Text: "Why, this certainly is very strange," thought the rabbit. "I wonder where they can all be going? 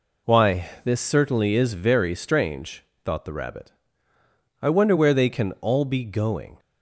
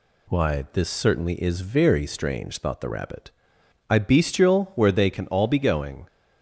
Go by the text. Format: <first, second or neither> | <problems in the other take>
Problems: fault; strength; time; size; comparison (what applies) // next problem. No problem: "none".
first | says "bestial" for "wonder"; at 3.9 s